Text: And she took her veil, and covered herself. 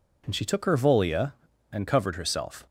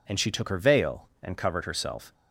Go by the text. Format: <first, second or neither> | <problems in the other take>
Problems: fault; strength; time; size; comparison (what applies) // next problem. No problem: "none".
second | says "volia" for "veil"; at 0.7 s